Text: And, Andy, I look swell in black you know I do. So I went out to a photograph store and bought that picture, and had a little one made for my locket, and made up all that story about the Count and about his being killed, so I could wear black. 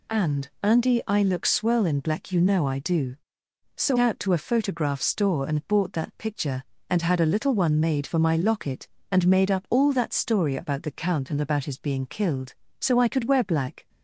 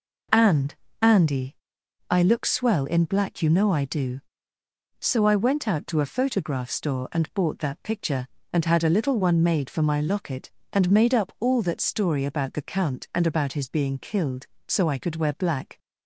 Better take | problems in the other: second | skips "I went"; at 3.9 s

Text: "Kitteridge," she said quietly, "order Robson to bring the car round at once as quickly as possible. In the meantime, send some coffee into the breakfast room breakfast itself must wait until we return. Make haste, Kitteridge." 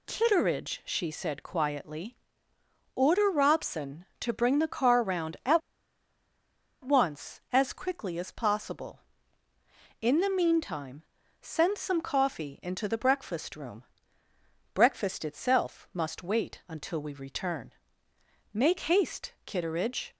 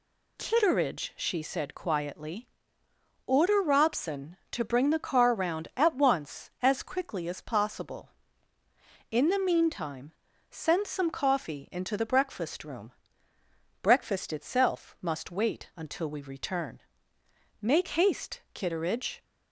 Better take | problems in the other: second | pauses between "at" and "once"; strong; at 5.6 s; 1.2 s long // pauses between "room" and "breakfast"; noticeable; at 13.8 s; 0.90 s long; noticeable in the second

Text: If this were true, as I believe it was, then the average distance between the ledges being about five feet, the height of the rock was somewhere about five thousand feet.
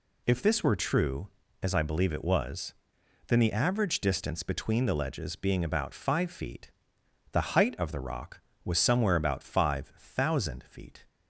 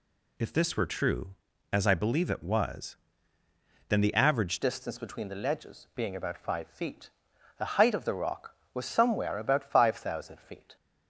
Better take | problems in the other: first | changes voice at "distance"; from 4.6 s on; 6.1 s long

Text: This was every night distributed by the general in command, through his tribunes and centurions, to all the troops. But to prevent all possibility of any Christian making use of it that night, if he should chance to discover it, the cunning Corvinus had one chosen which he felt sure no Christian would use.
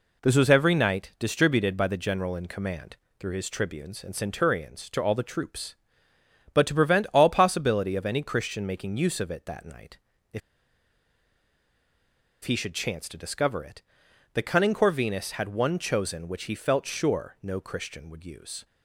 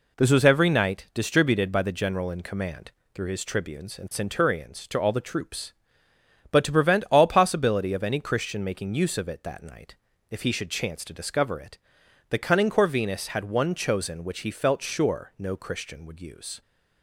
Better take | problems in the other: second | pauses between "if" and "he"; strong; at 10.4 s; 2.0 s long

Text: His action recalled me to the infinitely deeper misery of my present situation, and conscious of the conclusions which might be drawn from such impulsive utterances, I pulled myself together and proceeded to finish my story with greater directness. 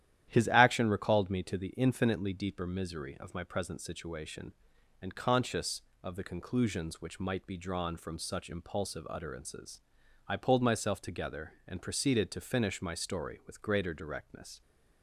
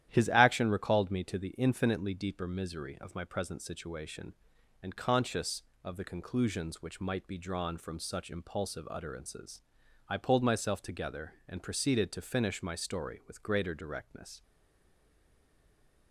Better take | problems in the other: first | starts louder than the rest; strong; until 1.1 s; 11.5 dB; strong in the first // stays silent after the last word; noticeable; from 14.4 s on; 1.7 s long

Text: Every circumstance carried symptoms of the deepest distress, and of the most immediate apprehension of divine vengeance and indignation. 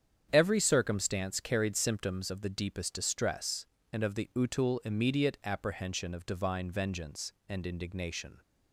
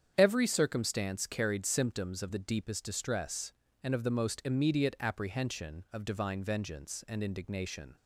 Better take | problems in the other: second | starts louder than the rest; strong; until 1.3 s; 8.5 dB; strong in the second // says "utul" for "most"; at 4.3 s

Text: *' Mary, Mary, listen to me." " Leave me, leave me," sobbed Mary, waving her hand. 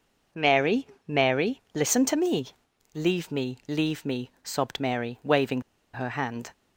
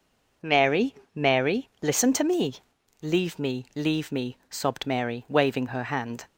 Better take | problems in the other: second | pauses between "waving" and "her"; slight; at 5.6 s; 0.33 s long

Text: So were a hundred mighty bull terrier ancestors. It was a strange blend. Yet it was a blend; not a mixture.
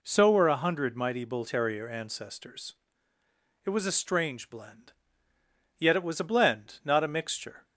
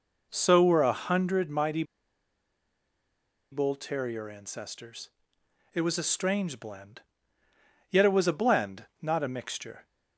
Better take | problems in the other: first | pauses between "mighty" and "bull"; strong; at 1.8 s; 1.6 s long

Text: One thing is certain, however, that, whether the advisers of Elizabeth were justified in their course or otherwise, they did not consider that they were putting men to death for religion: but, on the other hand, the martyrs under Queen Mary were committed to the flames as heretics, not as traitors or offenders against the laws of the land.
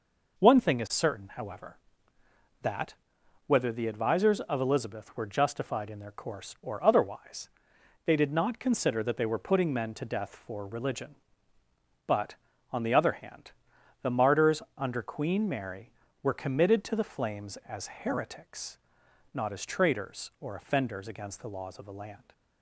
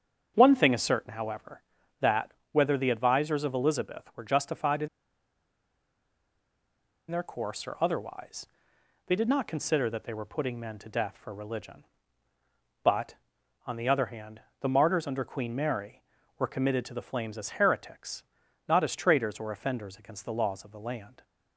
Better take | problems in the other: first | starts louder than the rest; strong; until 1.3 s; 7.5 dB // pauses between "in" and "their"; strong; at 4.8 s; 2.2 s long

